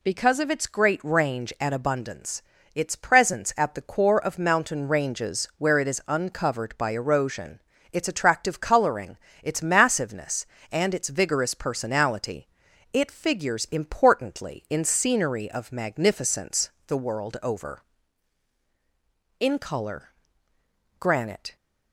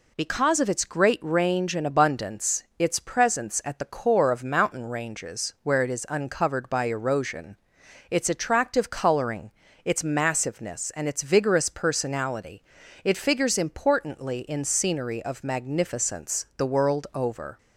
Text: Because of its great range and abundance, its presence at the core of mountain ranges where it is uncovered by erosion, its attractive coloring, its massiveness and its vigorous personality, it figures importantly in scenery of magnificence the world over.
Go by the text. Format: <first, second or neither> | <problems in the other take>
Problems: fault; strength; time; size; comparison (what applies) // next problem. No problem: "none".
second | pauses between "magnificence" and "the"; slight; at 16.7 s; 0.16 s long // goes on to say "In color granite"; strong; from 19.3 s on; 2.1 s long